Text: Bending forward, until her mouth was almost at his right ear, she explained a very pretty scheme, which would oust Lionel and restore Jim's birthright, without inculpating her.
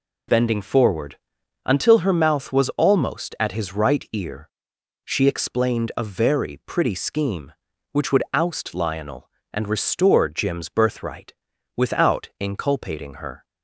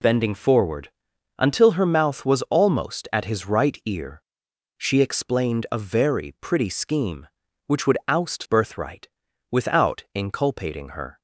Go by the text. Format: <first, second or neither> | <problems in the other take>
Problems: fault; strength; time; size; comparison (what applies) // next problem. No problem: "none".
first | skips "Lionel and restore Jim's"; at 8.4 s